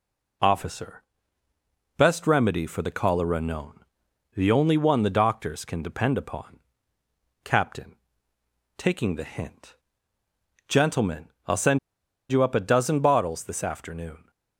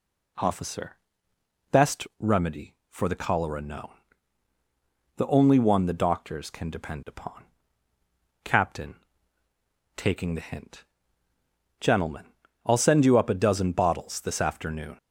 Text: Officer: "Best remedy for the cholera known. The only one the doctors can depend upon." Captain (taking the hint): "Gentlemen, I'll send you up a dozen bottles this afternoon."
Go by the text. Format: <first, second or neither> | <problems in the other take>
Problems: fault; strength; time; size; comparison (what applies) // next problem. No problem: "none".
second | pauses between "send" and "you"; noticeable; at 11.7 s; 0.51 s long